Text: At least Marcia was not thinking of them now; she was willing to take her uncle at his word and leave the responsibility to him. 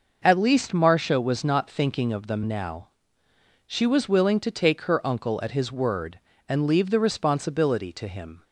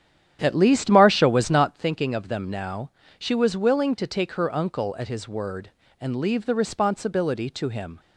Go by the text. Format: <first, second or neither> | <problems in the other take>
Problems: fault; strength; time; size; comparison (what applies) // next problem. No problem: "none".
first | starts louder than the rest; strong; until 1.8 s; 10 dB